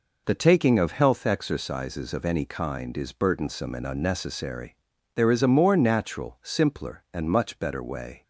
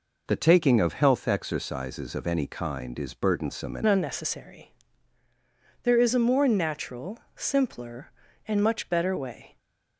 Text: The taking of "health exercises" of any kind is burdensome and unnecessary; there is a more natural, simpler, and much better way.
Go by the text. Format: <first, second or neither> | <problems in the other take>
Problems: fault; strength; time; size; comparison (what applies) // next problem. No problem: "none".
first | changes voice at "unnecessary"; from 3.8 s on; 5.7 s long // stays silent after the last word; slight; from 9.4 s on; 0.5 s long